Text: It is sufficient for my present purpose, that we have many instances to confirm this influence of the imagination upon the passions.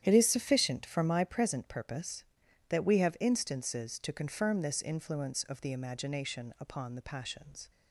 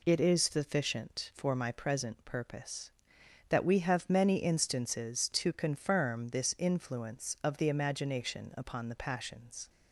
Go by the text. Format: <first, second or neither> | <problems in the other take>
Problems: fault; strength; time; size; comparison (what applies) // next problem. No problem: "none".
second | starts louder than the rest; strong; until 1.0 s; 10 dB // skips "many"; at 3.1 s